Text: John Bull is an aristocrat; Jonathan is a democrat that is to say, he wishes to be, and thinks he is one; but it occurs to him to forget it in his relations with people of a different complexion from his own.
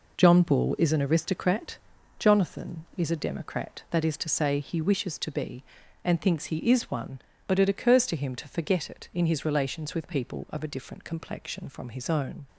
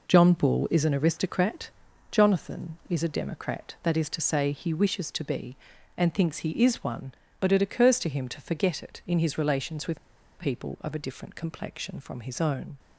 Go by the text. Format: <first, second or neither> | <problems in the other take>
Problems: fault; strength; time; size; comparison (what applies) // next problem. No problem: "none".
first | pauses between "with" and "people"; at 9.9 s; 0.39 s long